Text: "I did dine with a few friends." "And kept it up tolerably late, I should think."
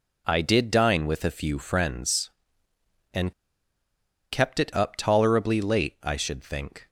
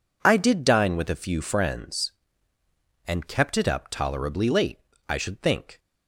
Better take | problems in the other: second | pauses between "And" and "kept"; at 3.3 s; 0.99 s long

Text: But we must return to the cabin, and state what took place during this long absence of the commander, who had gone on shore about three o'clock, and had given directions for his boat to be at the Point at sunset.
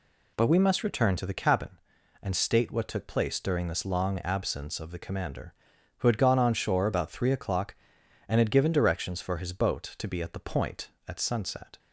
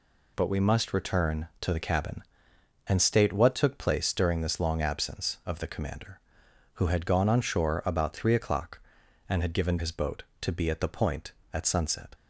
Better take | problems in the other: first | skips "directions for"; at 9.7 s

